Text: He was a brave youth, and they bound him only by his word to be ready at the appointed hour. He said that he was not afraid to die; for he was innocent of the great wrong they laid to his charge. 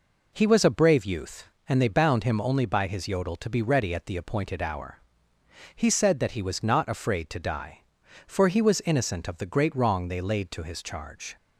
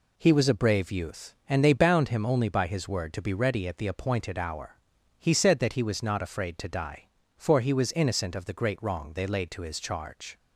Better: second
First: says "yodel" for "word"; at 3.0 s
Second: none

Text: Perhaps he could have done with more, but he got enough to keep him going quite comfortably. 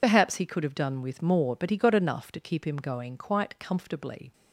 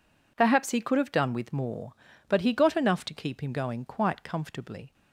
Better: second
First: loses the start of "Perhaps"; at 0.0 s; 65 ms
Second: none

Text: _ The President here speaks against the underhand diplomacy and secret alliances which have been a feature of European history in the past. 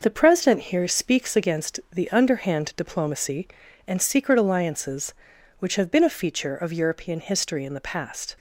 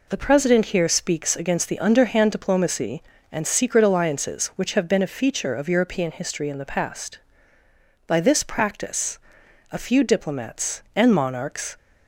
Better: first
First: none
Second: goes on to say "By this practice a few diplomats and monarchs"; strong; from 8.0 s on; 3.7 s long

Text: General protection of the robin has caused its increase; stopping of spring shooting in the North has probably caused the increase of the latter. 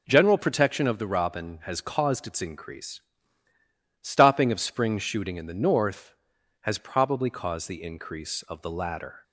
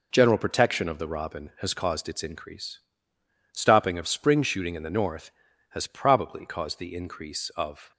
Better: first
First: none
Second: stops before "the latter"; at 7.9 s

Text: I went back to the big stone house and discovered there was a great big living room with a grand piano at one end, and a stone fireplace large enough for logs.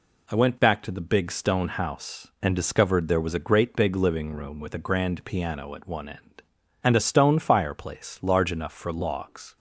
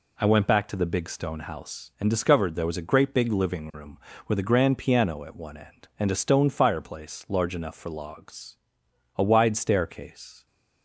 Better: first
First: none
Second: goes on to say "A wide staircase"; noticeable; from 9.1 s on; 1.3 s long

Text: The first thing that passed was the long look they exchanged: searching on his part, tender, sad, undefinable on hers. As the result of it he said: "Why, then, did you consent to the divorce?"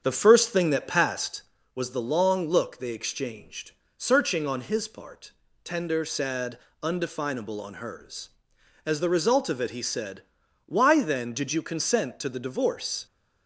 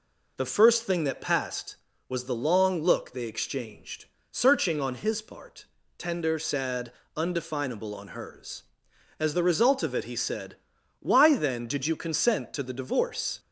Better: second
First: starts louder than the rest; strong; until 1.7 s; 7.5 dB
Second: none

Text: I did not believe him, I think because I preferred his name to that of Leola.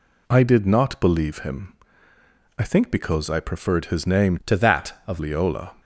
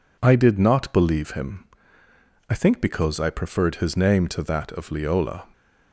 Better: second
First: changes voice from "to" to "of"; from 4.4 to 5.1 s; 0.7 s long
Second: none

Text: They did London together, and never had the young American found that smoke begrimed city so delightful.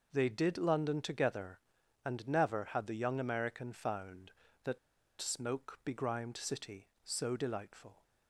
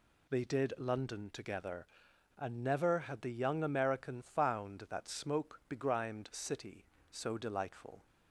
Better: second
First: pauses between "that" and "smoke"; at 4.7 s; 0.43 s long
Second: none

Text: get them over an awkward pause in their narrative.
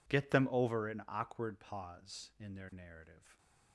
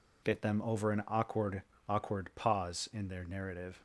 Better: first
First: none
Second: says "awkward" twice; at 1.8 s

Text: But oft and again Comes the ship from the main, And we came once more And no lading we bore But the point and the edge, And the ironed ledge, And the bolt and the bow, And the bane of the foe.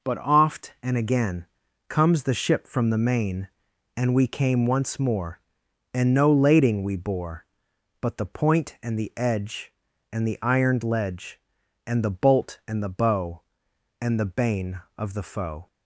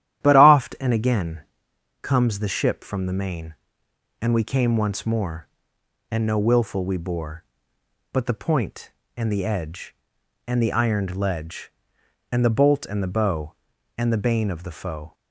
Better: first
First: pauses between "again" and "Comes"; at 1.4 s; 0.44 s long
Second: starts louder than the rest; strong; until 1.2 s; 12 dB // pauses between "again" and "Comes"; noticeable; at 1.3 s; 0.62 s long // says "willful" for "lading"; at 6.3 s

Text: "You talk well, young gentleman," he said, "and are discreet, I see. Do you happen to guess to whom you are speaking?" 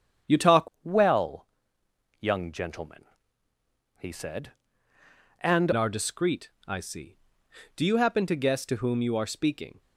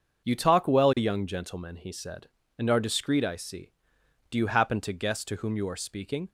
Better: second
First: starts louder than the rest; strong; until 1.4 s; 8.5 dB // changes voice from "well" to "and"; from 0.8 to 5.7 s; 4.9 s long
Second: starts louder than the rest; until 1.2 s; 6.5 dB

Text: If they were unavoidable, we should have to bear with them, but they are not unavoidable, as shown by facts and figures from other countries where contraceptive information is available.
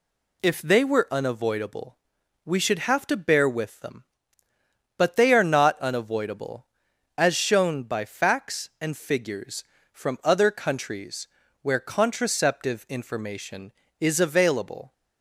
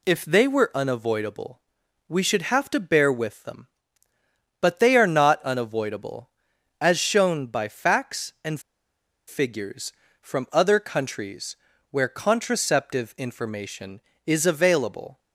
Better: first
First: pauses between "countries" and "where"; slight; at 11.2 s; 0.34 s long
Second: pauses between "and" and "figures"; noticeable; at 8.5 s; 0.68 s long // pauses between "countries" and "where"; slight; at 11.5 s; 0.34 s long

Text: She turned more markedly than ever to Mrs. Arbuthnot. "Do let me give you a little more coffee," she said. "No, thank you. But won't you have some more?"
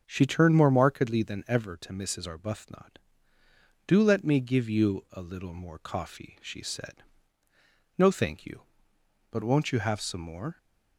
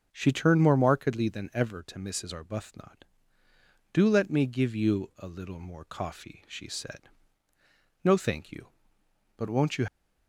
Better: first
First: starts louder than the rest; until 1.0 s; 6.5 dB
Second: starts louder than the rest; until 1.1 s; 6.5 dB // stops before "have some more"; at 9.8 s

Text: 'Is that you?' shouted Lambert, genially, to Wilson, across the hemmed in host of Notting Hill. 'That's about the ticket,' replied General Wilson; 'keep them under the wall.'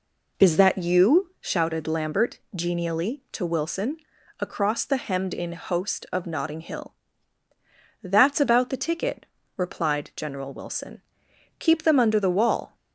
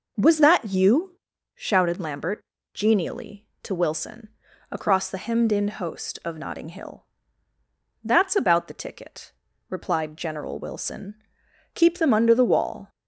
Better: first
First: none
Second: says "Was" for "Is"; at 0.1 s

